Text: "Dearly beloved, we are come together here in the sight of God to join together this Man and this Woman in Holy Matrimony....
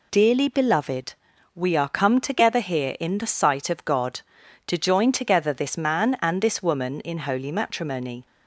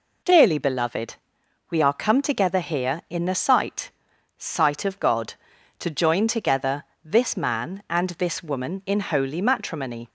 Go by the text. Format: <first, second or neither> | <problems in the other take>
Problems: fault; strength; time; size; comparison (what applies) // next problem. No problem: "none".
first | says "sight" twice; at 4.3 s // pauses between "together" and "this"; slight; at 6.8 s; 0.18 s long